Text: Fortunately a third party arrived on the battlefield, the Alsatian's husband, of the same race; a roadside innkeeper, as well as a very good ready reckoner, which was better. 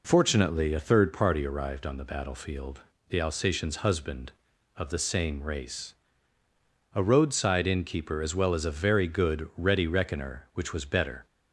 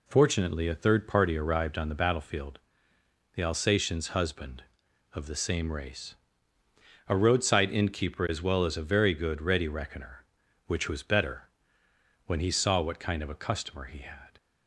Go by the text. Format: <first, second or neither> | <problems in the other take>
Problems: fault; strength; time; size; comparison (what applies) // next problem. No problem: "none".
first | goes on to say "When he saw what kind of a customer he had"; strong; from 12.2 s on; 2.0 s long